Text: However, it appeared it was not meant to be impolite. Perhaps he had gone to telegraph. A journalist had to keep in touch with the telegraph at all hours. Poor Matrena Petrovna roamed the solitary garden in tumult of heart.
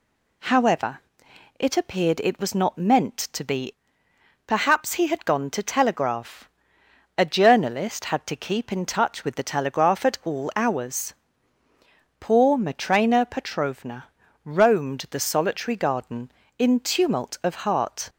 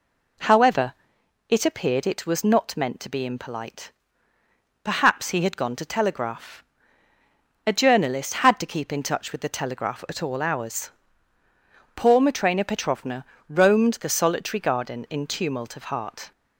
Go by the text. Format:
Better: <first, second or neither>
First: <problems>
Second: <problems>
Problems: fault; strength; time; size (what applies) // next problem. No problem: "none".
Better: second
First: skips "impolite"; at 4.0 s // pauses between "Petrovna" and "roamed"; slight; at 14.0 s; 0.36 s long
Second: pauses between "Petrovna" and "roamed"; slight; at 13.2 s; 0.24 s long